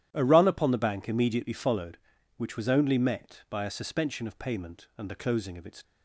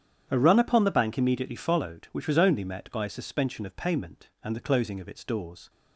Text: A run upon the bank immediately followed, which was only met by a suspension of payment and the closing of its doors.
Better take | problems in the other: second | starts louder than the rest; strong; until 1.1 s; 11.5 dB; strong in the second // stops before "doors"; at 5.8 s

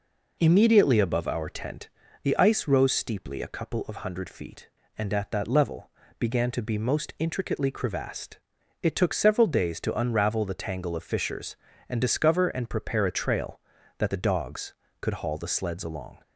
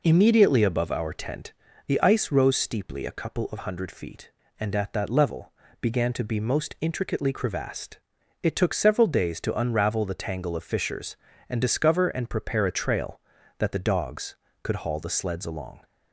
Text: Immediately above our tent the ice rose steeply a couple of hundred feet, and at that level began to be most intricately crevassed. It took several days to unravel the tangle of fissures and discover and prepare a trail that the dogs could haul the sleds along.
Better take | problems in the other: neither | pauses between "tent" and "the"; slight; the same in both // pauses between "level" and "began"; slight; the same in both

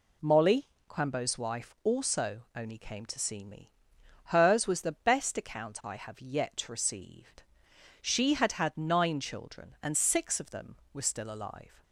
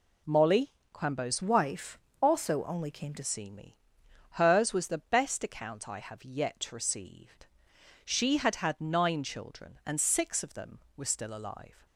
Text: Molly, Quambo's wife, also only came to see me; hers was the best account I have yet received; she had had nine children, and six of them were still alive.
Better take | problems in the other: first | changes voice from "wife" to "to"; from 1.4 to 3.2 s; 1.8 s long

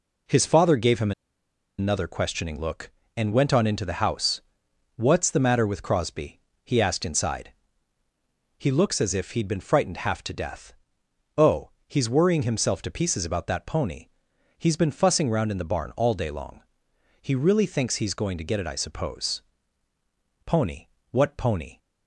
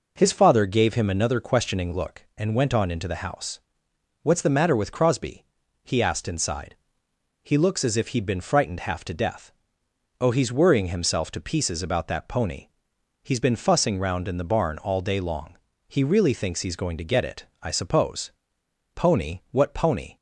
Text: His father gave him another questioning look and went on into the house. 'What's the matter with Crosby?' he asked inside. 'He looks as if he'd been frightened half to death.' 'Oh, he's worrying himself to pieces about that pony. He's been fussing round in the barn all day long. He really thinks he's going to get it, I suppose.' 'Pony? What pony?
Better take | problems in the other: second | pauses between "him" and "another"; noticeable; at 1.1 s; 0.67 s long

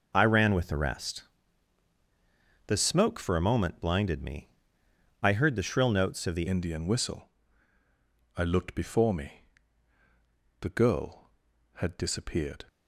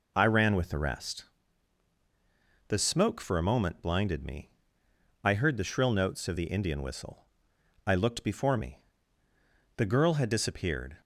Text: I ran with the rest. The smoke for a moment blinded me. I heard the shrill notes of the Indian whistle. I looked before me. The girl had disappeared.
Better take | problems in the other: second | changes voice at "Indian"; from 6.4 s on; 6.2 s long

